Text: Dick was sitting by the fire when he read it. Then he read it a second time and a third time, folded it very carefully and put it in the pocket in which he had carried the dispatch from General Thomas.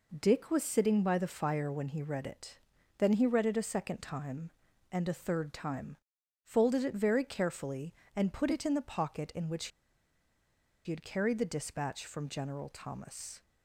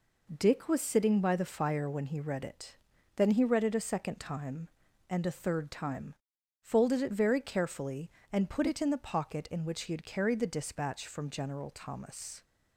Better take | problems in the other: second | pauses between "which" and "he"; at 9.6 s; 1.1 s long

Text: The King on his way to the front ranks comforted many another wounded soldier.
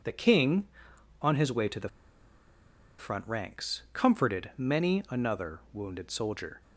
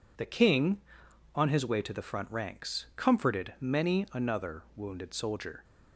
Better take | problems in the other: second | pauses between "the" and "front"; at 1.8 s; 1.1 s long

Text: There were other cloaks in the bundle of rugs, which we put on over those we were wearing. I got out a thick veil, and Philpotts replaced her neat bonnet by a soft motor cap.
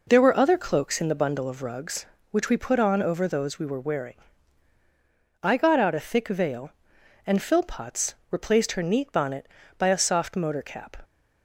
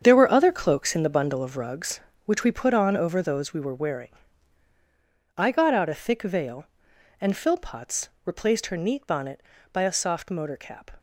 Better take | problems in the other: first | gets quieter; strong; throughout; 10.5 dB // pauses between "Philpotts" and "replaced"; slight; at 8.0 s; 0.16 s long; slight in the first

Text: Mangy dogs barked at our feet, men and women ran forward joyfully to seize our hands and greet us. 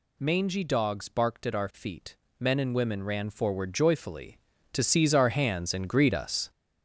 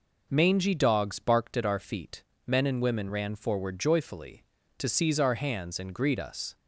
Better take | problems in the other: second | gets louder; throughout; 7 dB

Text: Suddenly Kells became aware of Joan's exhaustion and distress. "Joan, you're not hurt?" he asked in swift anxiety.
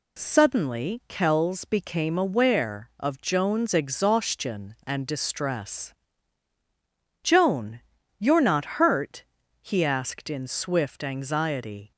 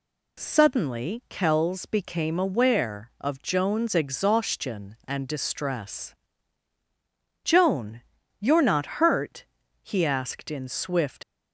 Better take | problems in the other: first | stops before "anxiety"; at 11.2 s

